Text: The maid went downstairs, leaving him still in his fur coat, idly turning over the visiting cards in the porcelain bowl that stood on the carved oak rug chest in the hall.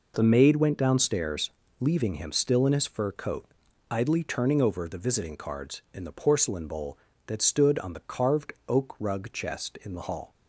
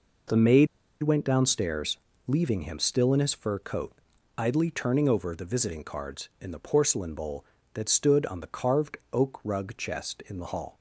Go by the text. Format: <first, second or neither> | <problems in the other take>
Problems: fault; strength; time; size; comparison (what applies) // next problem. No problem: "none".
first | pauses between "maid" and "went"; slight; at 0.6 s; 0.35 s long // pauses between "carved" and "oak"; slight; at 8.9 s; 0.16 s long; slight in the first